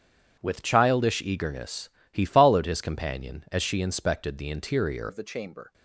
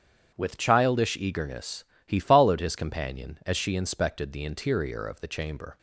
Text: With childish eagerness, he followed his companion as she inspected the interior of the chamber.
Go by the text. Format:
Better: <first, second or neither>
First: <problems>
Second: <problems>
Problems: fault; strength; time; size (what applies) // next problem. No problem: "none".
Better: second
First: starts louder than the rest; strong; until 1.4 s; 8.5 dB // changes voice at "of"; from 5.0 s on; 0.7 s long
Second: starts louder than the rest; strong; until 1.4 s; 8.5 dB